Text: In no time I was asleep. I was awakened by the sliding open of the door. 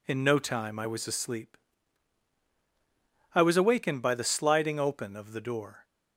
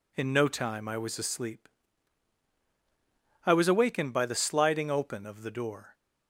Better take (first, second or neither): neither